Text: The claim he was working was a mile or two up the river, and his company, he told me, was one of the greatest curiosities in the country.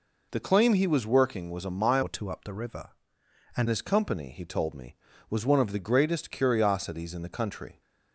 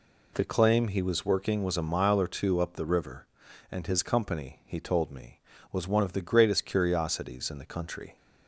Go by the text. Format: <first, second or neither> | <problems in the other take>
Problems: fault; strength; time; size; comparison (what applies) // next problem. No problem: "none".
second | changes voice from "or" to "and"; from 2.0 to 3.6 s; 1.6 s long